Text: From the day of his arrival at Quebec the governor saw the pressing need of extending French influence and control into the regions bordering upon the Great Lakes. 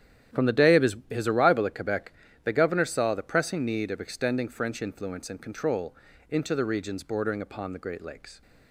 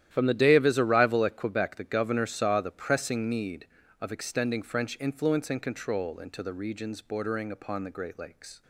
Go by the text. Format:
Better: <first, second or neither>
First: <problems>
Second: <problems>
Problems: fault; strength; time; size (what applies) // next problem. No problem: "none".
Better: second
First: starts louder than the rest; strong; until 1.4 s; 11 dB // says "his" twice; at 1.0 s // pauses between "Quebec" and "the"; slight; at 2.1 s; 0.32 s long // pauses between "control" and "into"; slight; at 5.9 s; 0.36 s long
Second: starts louder than the rest; strong; until 1.1 s; 11.5 dB